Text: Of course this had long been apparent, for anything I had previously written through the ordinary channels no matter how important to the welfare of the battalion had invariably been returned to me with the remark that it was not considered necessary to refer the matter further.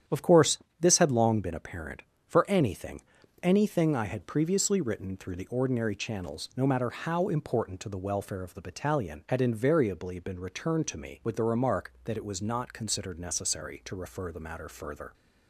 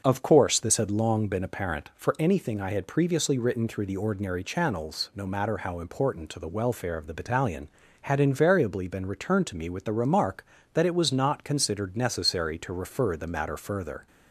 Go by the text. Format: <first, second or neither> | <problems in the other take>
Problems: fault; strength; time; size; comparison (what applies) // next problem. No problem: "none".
second | starts louder than the rest; strong; until 1.3 s; 9.5 dB; noticeable in the second // pauses between "course" and "this"; slight; at 0.5 s; 0.22 s long // says "anything" twice; at 3.4 s